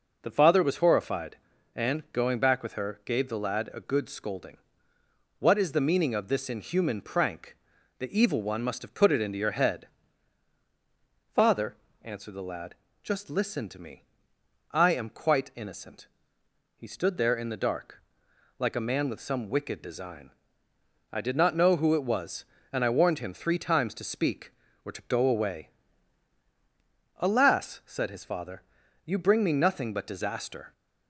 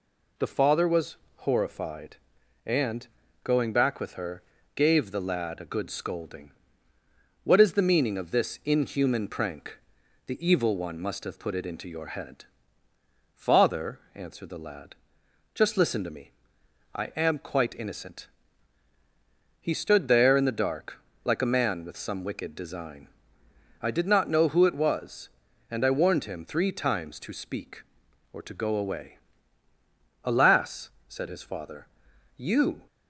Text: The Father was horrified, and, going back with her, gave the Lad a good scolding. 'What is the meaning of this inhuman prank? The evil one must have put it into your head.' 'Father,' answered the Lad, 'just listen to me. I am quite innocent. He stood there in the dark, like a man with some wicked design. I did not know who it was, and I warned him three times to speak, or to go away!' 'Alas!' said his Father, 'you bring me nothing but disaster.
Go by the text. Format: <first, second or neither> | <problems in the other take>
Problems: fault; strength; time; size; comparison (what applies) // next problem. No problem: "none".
first | pauses between "was" and "horrified"; slight; at 1.1 s; 0.22 s long // stops before "bring me nothing but disaster"; at 32.8 s